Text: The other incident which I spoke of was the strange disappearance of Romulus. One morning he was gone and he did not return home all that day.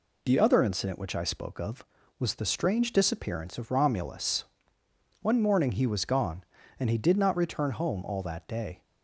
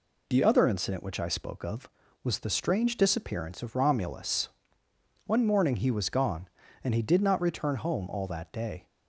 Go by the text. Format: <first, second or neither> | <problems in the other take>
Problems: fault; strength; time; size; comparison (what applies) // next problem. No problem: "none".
neither | none